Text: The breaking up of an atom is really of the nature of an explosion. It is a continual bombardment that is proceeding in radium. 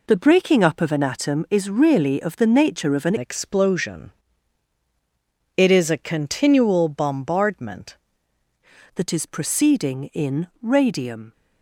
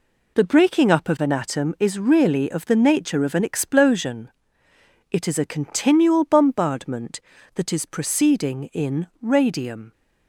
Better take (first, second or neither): second